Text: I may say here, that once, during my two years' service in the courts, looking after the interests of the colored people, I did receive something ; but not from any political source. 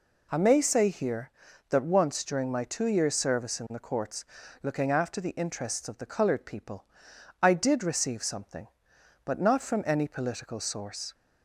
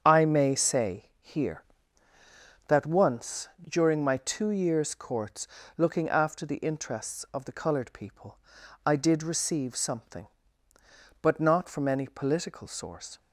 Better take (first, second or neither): first